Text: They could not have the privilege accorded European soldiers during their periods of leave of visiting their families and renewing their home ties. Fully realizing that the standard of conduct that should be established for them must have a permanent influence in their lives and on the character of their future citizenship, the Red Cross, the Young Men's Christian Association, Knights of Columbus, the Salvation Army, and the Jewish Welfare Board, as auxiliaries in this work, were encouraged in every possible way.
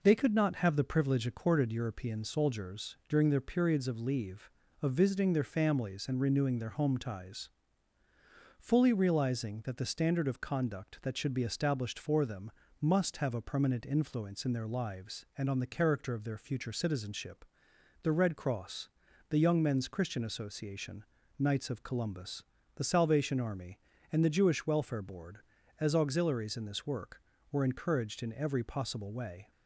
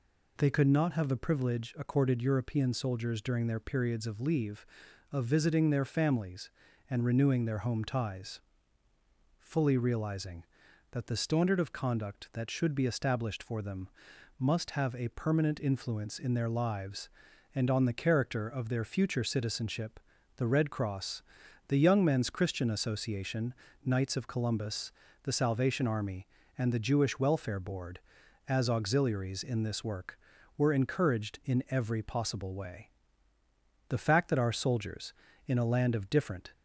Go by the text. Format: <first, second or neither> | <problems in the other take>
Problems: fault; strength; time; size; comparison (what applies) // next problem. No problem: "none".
first | pauses between "them" and "must"; noticeable; at 13.8 s; 0.50 s long; slight in the first // goes on to say "The fact that our soldiers in a land of different"; strong; from 33.8 s on; 2.6 s long